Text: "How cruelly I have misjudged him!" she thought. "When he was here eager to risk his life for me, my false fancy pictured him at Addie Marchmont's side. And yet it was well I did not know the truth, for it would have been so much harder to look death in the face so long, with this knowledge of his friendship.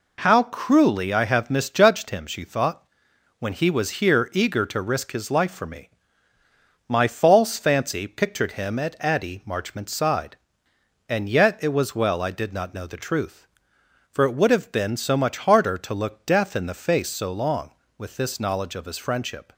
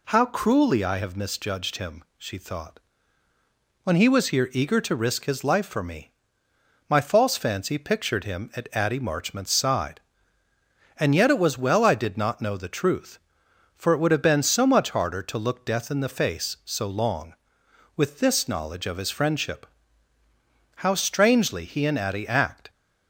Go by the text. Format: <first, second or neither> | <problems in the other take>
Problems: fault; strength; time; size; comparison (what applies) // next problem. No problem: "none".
first | goes on to say "How strangely he and Addie act"; strong; from 20.7 s on; 1.9 s long